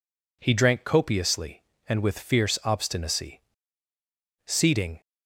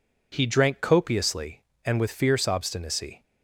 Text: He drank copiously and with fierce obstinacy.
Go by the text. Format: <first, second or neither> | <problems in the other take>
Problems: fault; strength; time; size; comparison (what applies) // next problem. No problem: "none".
second | goes on to say "Seating"; from 4.4 s on; 0.54 s long